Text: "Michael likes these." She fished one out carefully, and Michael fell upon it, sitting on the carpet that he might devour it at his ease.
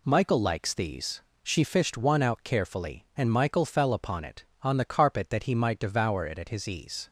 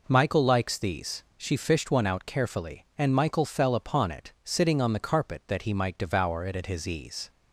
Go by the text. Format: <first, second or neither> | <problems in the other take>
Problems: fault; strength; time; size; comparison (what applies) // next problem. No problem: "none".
second | skips "sitting"; at 4.5 s